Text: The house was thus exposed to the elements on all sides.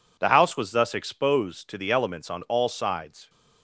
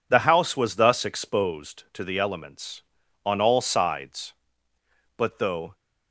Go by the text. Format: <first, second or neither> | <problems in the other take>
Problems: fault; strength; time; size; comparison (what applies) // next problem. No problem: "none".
first | goes on to say "But though"; from 5.1 s on; 0.58 s long